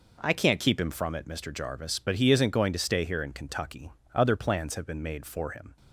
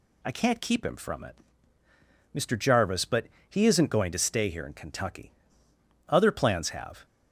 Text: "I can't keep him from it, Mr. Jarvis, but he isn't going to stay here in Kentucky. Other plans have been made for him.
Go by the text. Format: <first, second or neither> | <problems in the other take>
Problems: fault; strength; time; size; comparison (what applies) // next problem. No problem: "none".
first | pauses between "but" and "he"; slight; at 3.2 s; 0.20 s long // stops before "been made for him"; at 7.0 s